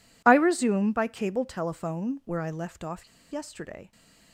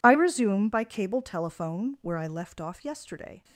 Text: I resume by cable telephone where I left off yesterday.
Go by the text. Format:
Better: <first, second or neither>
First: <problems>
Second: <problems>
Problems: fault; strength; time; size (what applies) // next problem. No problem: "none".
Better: second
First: pauses between "off" and "yesterday"; slight; at 3.0 s; 0.23 s long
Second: none